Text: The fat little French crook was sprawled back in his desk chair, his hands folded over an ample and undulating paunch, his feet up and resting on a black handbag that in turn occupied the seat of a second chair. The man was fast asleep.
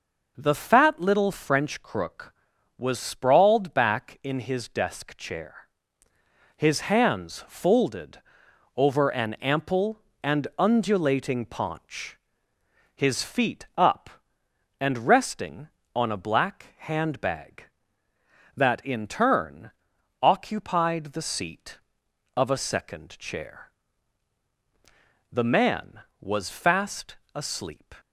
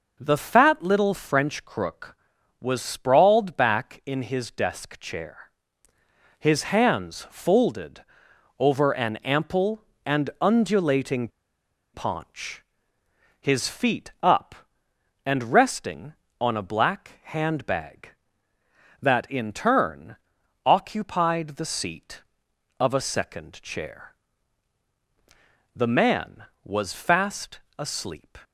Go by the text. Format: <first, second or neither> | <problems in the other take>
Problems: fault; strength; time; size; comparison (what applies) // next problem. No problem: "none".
first | pauses between "folded" and "over"; noticeable; at 8.0 s; 0.56 s long; noticeable in the first // pauses between "undulating" and "paunch"; noticeable; at 11.2 s; 0.65 s long // pauses between "turn" and "occupied"; noticeable; at 20.1 s; 0.50 s long; noticeable in the first // pauses between "fast" and "asleep"; slight; at 27.5 s; 0.18 s long; slight in the first